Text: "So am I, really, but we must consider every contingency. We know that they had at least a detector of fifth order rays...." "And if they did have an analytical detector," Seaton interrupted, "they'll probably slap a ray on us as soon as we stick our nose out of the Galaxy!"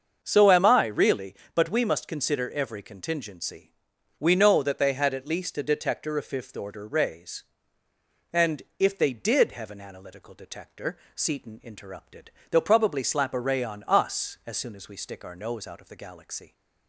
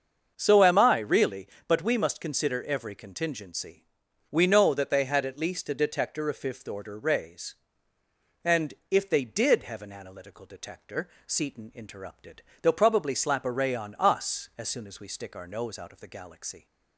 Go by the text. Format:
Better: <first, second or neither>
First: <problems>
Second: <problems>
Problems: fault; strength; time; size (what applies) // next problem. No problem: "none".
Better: neither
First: starts louder than the rest; until 1.2 s; 6.5 dB // pauses between "And" and "if"; slight; at 8.6 s; 0.16 s long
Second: starts louder than the rest; until 1.3 s; 6.5 dB // pauses between "And" and "if"; slight; at 8.7 s; 0.16 s long